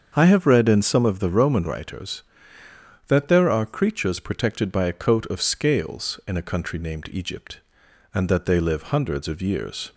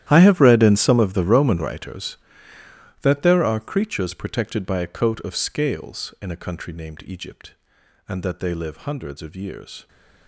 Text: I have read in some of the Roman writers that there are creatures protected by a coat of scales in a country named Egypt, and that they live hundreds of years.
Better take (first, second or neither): first